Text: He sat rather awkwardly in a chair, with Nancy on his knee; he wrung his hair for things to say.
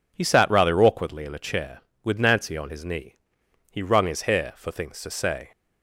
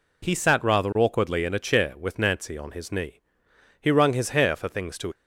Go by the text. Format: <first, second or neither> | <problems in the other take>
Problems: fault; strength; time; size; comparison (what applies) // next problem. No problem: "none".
first | stops before "say"; at 5.1 s